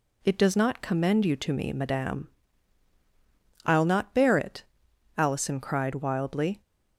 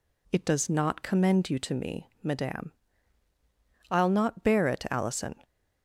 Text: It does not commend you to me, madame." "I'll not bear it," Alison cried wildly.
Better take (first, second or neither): first